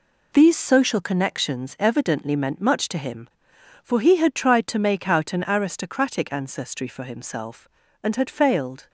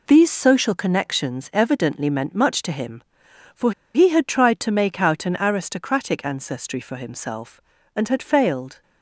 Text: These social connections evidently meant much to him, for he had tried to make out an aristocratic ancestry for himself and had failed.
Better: first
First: none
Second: pauses between "for" and "he"; slight; at 3.7 s; 0.21 s long

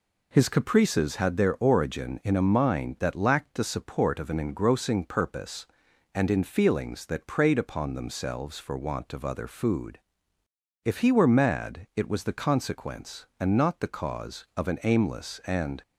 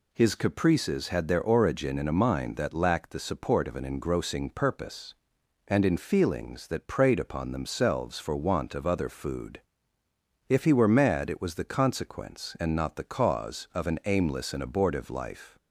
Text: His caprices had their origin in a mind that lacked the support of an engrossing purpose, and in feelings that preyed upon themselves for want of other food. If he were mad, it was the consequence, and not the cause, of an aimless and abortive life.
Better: second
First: stops before "abortive life"; at 15.8 s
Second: none

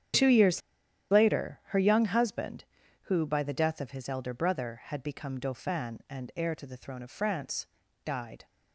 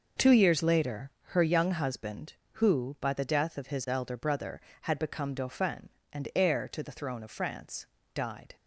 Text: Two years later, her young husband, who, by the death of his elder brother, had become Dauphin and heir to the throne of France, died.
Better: second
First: starts louder than the rest; strong; until 1.7 s; 9 dB // pauses between "years" and "later"; noticeable; at 0.6 s; 0.50 s long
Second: none

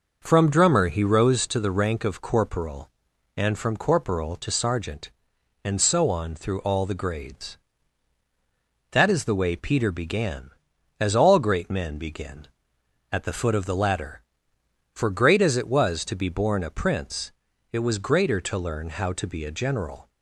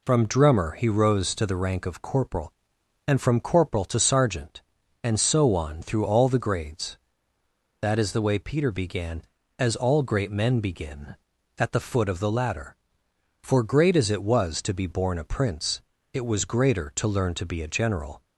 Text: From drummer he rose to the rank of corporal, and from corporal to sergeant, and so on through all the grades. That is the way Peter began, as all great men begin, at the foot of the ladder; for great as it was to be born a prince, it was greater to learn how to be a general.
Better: first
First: none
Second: skips "how"; at 17.3 s

